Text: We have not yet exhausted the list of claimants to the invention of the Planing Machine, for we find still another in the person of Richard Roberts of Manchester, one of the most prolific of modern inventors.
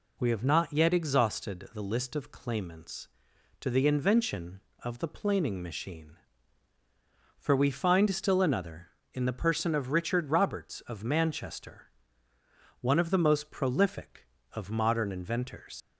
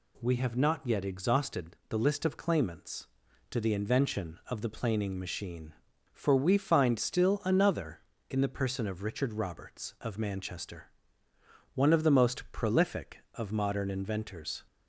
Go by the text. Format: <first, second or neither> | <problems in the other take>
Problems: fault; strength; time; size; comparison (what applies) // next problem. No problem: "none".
second | leaves "inventors" unfinished; at 15.8 s; 90 ms